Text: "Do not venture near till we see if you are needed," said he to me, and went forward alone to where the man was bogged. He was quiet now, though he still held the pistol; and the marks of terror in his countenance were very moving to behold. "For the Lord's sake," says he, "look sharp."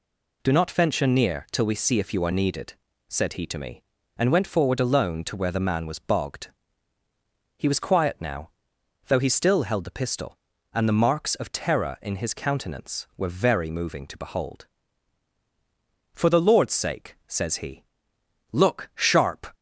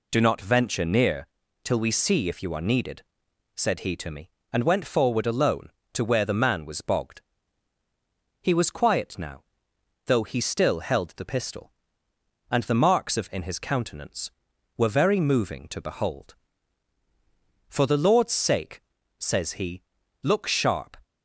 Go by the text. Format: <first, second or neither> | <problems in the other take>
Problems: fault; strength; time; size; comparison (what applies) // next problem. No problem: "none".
first | pauses between "near" and "till"; slight; at 1.2 s; 0.36 s long // skips "terror"; at 13.3 s